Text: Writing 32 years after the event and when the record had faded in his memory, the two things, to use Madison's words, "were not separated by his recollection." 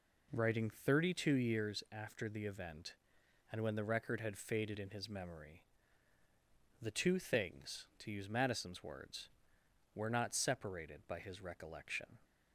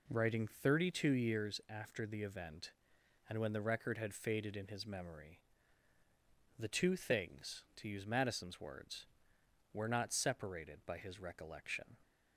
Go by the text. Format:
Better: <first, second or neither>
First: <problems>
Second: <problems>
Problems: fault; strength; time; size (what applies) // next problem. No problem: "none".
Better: neither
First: none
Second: none